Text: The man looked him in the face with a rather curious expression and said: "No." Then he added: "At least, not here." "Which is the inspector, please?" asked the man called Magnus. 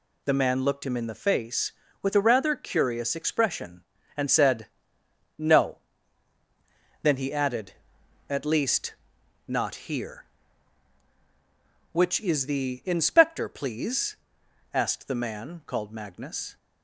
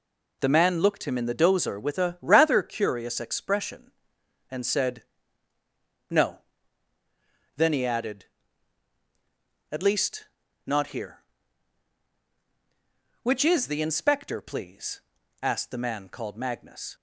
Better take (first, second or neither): first